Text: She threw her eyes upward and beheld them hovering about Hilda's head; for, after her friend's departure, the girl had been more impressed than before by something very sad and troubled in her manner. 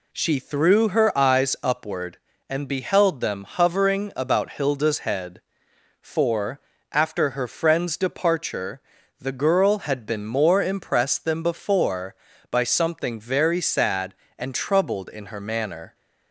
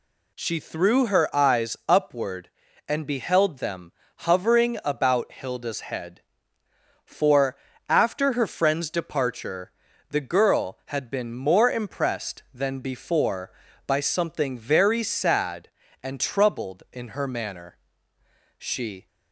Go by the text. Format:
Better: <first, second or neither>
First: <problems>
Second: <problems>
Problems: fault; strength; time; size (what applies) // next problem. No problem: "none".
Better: first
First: none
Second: pauses between "them" and "hovering"; slight; at 3.9 s; 0.26 s long // goes on to say "She"; from 18.5 s on; 0.50 s long